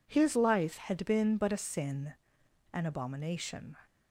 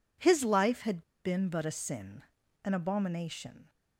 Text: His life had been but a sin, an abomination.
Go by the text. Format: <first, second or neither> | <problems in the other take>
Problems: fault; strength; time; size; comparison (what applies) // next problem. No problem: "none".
first | pauses between "had" and "been"; slight; at 1.0 s; 0.22 s long